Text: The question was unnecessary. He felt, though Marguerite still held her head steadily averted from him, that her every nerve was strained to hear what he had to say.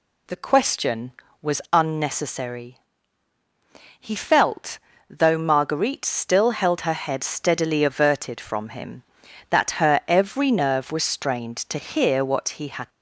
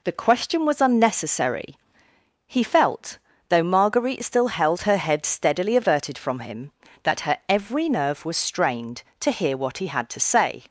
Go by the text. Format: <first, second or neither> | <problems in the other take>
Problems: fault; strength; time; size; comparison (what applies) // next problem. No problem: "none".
second | stops before "to say"; at 12.8 s